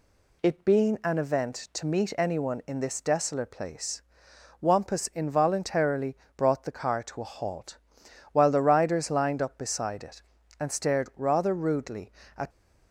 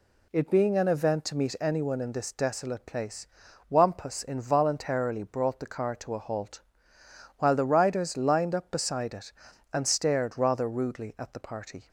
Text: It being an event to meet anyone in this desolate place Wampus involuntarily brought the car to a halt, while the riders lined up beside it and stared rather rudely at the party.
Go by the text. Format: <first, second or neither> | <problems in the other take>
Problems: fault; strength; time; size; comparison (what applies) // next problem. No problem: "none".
second | pauses between "place" and "Wampus"; noticeable; at 4.0 s; 0.60 s long; also in the second // pauses between "involuntarily" and "brought"; slight; at 6.1 s; 0.22 s long // stops before "the party"; at 12.4 s